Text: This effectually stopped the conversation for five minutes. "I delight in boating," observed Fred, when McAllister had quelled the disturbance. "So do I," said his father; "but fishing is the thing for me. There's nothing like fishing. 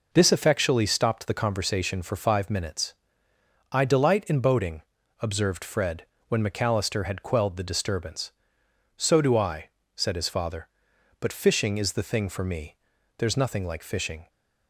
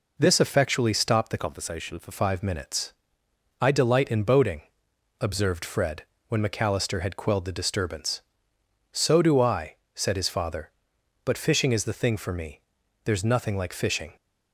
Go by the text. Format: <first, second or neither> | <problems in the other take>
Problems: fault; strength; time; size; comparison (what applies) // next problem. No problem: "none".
first | changes voice from "conversation" to "for"; from 1.3 to 2.1 s; 0.8 s long